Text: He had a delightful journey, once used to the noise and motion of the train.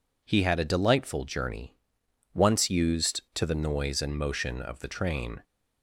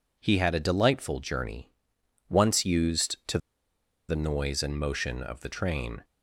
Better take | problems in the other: first | pauses between "to" and "the"; noticeable; at 3.3 s; 0.70 s long

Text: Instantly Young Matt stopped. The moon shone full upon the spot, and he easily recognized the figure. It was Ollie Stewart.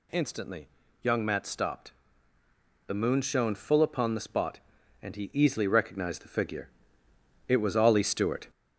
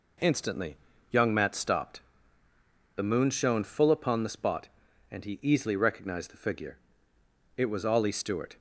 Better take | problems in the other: second | gets louder; throughout; 3.5 dB // pauses between "Instantly" and "Young"; slight; at 0.6 s; 0.36 s long; slight in the second

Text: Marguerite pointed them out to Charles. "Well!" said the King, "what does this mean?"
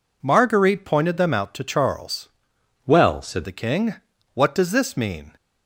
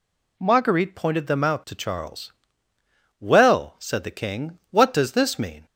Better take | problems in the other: second | changes voice from "Well" to "said"; from 2.8 to 3.4 s; 0.6 s long

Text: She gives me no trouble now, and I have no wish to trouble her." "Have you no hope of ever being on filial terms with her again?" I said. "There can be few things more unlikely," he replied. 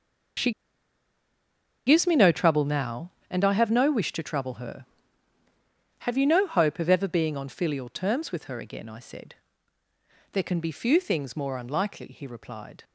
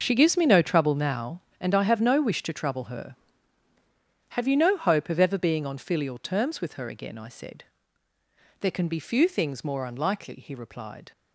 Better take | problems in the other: second | pauses between "She" and "gives"; strong; at 0.5 s; 1.3 s long

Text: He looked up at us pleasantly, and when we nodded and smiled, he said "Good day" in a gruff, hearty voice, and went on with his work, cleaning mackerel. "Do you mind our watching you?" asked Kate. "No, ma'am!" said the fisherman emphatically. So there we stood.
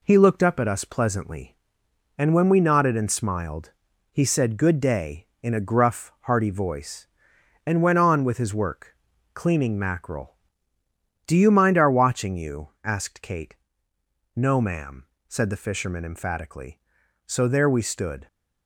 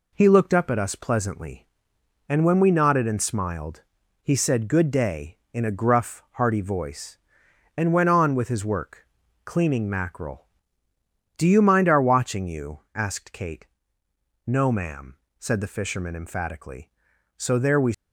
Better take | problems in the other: first | stops before "stood"; at 17.9 s

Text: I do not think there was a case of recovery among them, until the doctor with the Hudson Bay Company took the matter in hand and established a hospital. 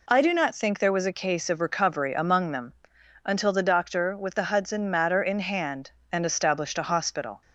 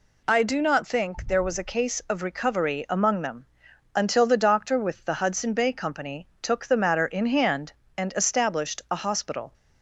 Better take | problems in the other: second | skips "Bay Company took the"; at 4.9 s

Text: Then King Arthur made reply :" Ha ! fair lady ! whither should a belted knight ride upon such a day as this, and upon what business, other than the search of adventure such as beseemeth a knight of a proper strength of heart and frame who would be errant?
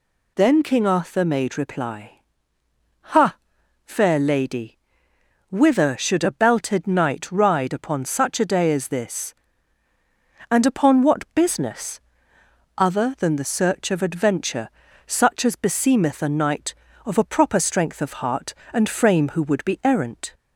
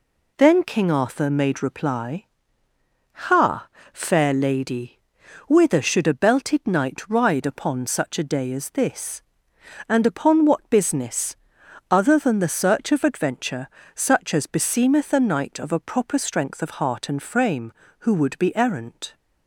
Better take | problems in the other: second | gets louder; slight; throughout; 2.5 dB // pauses between "adventure" and "such"; slight; at 14.6 s; 0.36 s long; slight in the second

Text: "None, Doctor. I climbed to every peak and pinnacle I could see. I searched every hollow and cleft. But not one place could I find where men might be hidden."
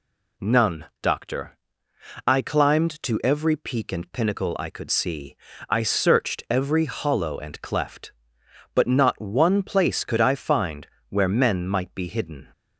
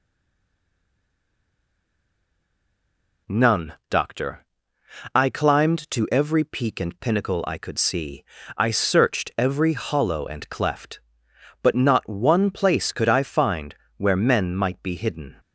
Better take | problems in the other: first | stays silent before the first word; strong; until 3.2 s; 3.2 s long // pauses between "find" and "where"; slight; at 13.7 s; 0.22 s long; slight in the first

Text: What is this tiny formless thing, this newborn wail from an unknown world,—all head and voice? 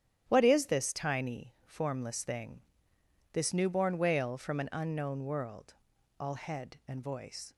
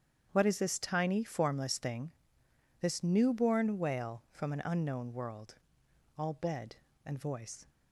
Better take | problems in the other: first | starts louder than the rest; strong; until 1.3 s; 8.5 dB; strong in the first // says "bed" for "head"; at 6.3 s

